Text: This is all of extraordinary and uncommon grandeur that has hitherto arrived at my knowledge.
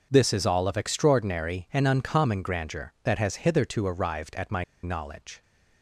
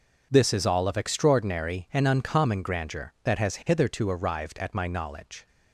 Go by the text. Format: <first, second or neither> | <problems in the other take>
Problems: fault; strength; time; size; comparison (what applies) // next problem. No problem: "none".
second | pauses between "my" and "knowledge"; slight; at 4.6 s; 0.19 s long